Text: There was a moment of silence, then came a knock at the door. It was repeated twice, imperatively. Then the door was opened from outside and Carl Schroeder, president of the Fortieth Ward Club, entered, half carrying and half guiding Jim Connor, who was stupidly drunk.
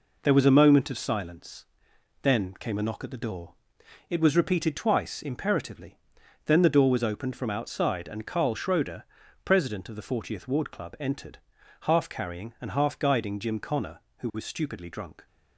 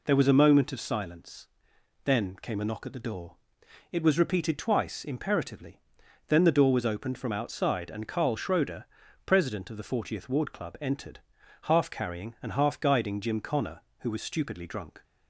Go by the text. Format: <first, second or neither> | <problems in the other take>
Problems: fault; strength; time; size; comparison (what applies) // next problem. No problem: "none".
second | gets quieter; noticeable; throughout; 6 dB